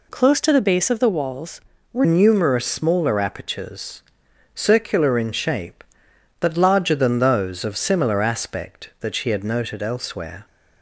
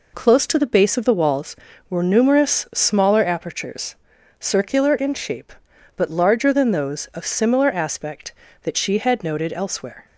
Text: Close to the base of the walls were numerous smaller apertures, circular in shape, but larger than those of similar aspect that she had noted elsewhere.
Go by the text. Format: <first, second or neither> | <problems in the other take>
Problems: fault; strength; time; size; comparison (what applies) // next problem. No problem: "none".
second | changes voice at "numerous"; from 2.0 s on; 8.4 s long